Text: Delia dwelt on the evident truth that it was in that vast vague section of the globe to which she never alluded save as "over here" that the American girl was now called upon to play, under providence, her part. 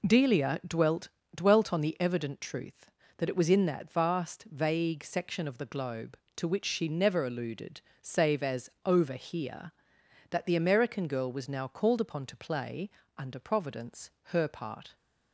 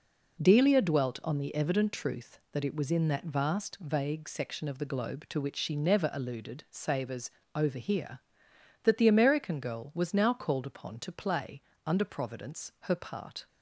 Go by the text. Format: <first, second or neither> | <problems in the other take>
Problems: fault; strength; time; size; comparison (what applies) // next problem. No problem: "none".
second | says "dwelt" twice; at 1.3 s // pauses between "alluded" and "save"; slight; at 7.8 s; 0.20 s long // pauses between "as" and "over"; slight; at 8.6 s; 0.16 s long; slight in the second